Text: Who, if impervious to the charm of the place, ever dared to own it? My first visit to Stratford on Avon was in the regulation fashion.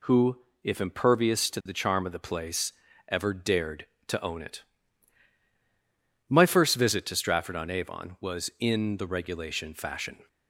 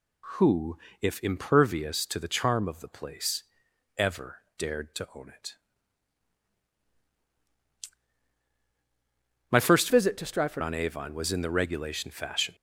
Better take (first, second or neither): first